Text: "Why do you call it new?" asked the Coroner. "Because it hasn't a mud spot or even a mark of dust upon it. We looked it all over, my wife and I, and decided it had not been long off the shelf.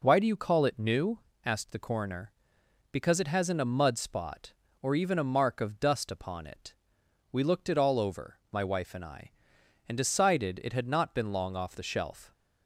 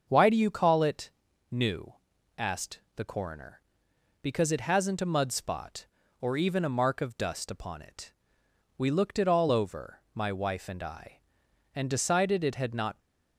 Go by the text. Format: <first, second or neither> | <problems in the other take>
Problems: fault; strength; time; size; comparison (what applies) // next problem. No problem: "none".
first | starts louder than the rest; until 1.0 s; 6.5 dB // pauses between "it" and "new"; at 1.1 s; 0.40 s long // pauses between "asked" and "the"; slight; at 2.7 s; 0.16 s long // stops before "been long off the shelf"; at 12.9 s